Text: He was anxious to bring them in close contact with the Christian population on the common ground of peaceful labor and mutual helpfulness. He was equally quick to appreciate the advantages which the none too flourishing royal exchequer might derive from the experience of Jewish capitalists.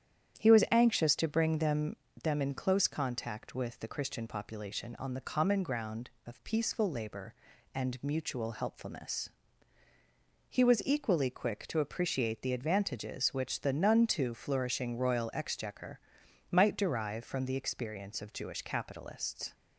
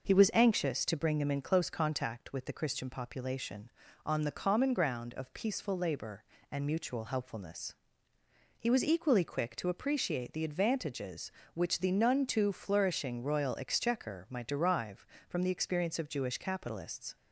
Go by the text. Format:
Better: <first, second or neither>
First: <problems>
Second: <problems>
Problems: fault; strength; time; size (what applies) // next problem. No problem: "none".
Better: second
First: starts louder than the rest; strong; until 1.4 s; 9.5 dB // says "them" twice; at 2.2 s // pauses between "exchequer" and "might"; noticeable; at 15.9 s; 0.50 s long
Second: none